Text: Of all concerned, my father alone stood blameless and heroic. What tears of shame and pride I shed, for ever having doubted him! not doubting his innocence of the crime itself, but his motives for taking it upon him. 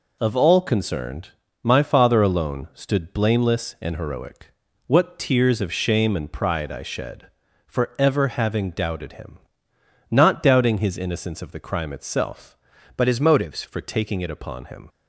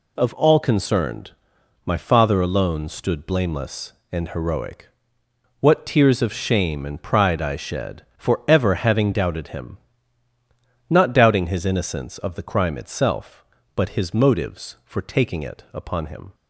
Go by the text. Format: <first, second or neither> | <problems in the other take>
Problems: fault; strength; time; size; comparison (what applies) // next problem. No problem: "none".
second | changes voice from "but" to "motives"; from 12.9 to 13.6 s; 0.7 s long